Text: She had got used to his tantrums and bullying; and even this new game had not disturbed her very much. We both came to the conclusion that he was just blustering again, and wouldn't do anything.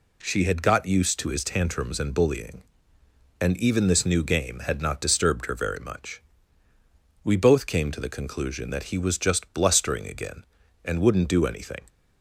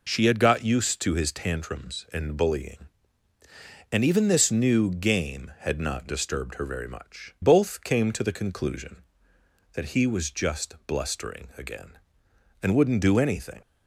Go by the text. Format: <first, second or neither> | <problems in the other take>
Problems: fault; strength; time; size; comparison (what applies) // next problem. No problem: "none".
first | skips "We"; at 7.3 s